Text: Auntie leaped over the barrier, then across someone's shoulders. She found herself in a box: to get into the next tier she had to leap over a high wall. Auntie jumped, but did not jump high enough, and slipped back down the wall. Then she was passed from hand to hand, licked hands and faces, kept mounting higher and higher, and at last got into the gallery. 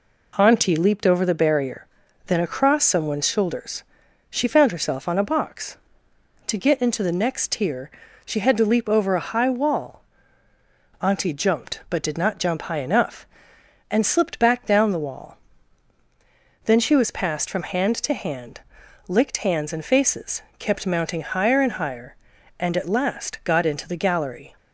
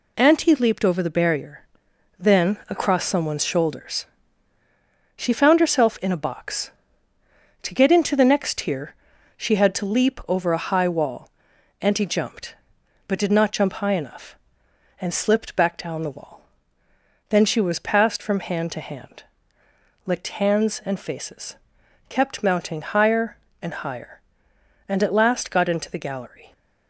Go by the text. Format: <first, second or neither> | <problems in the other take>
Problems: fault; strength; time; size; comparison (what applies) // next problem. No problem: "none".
second | says "on" for "in"; at 5.0 s // pauses between "tier" and "she"; at 7.8 s; 0.38 s long; also in the second